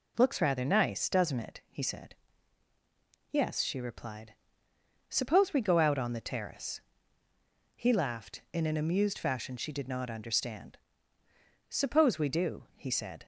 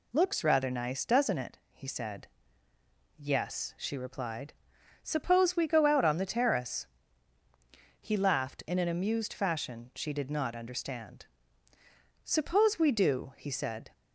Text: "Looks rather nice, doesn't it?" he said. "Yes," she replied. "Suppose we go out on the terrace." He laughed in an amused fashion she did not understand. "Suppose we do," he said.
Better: neither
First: none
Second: none

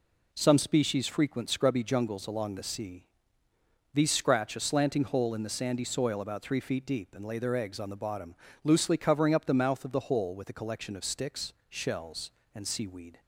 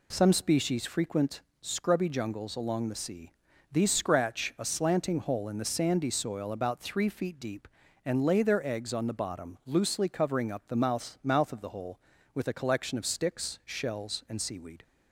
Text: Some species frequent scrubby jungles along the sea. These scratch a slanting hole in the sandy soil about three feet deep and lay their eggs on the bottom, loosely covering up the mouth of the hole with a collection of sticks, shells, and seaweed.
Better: first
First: none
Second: pauses between "frequent" and "scrubby"; slight; at 1.3 s; 0.22 s long // says "mouth" twice; at 11.2 s

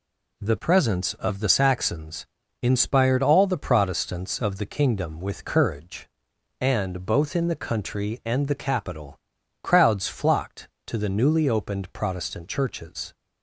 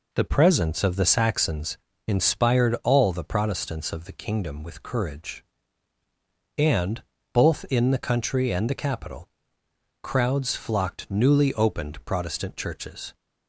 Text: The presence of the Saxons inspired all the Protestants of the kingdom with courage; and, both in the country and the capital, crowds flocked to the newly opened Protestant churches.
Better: first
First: pauses between "Saxons" and "inspired"; slight; at 2.2 s; 0.36 s long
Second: pauses between "Saxons" and "inspired"; slight; at 1.7 s; 0.28 s long // skips "to the"; at 11.0 s

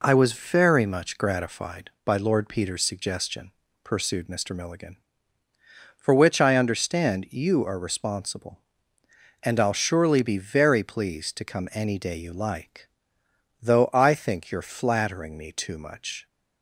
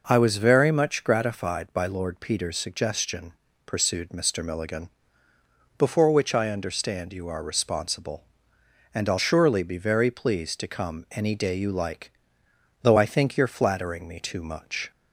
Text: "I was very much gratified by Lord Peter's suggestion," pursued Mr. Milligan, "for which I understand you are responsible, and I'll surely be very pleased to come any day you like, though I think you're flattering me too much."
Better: first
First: none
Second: says "before" for "for"; at 5.7 s

